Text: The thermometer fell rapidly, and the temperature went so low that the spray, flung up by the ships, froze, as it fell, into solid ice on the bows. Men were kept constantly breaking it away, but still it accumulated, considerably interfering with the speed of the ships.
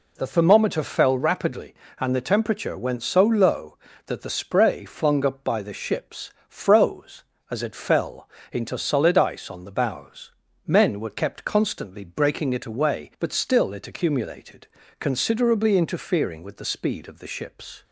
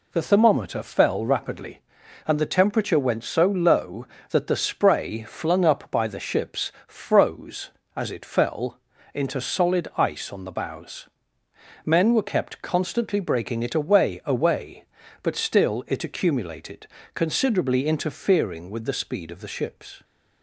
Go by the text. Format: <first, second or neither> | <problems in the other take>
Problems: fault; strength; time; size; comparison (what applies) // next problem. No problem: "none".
first | says "away" twice; at 14.2 s